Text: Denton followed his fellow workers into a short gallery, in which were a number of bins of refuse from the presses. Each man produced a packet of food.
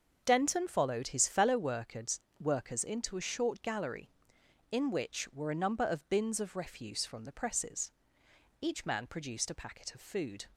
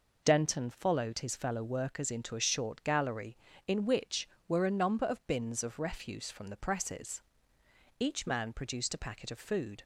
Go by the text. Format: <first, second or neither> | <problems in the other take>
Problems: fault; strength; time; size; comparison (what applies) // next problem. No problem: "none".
second | starts louder than the rest; until 1.2 s; 6.5 dB // says "workers" twice; at 2.3 s